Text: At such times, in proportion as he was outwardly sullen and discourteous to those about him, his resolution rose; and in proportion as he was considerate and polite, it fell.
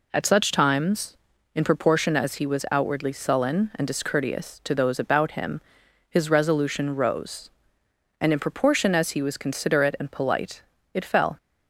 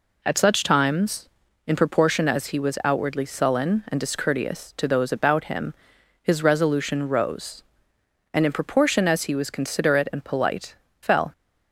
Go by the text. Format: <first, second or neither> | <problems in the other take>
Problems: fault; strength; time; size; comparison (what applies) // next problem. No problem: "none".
first | skips "it"; at 10.8 s